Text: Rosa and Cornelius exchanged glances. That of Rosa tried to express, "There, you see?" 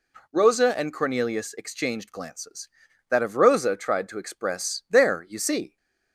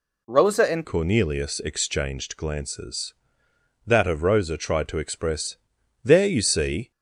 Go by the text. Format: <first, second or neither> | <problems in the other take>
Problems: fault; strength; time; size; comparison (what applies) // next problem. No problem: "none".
first | changes voice at "Cornelius"; from 0.8 s on; 6.1 s long